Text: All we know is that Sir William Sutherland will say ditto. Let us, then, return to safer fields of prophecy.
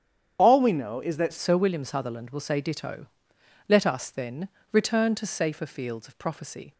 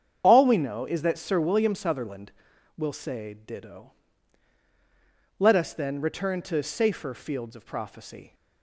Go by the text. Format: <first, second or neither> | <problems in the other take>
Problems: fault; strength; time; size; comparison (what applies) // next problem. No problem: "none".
second | starts louder than the rest; strong; until 1.4 s; 8.5 dB; strong in the second // changes voice at "Sir"; from 1.3 s on; 5.4 s long